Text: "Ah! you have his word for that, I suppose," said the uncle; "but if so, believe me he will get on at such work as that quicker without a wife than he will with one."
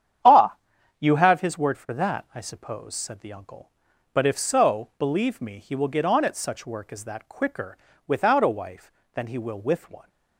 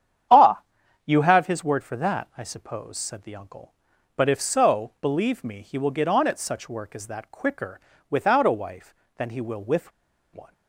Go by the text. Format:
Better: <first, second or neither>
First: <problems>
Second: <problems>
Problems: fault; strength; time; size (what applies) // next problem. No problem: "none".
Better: first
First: starts louder than the rest; strong; until 1.6 s; 9 dB // pauses between "quicker" and "without"; slight; at 7.7 s; 0.32 s long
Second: starts louder than the rest; strong; until 1.7 s; 9 dB // pauses between "quicker" and "without"; slight; at 7.7 s; 0.32 s long // pauses between "with" and "one"; at 9.9 s; 0.43 s long